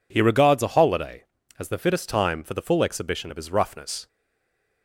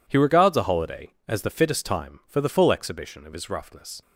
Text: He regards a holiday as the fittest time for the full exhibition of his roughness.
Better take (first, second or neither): second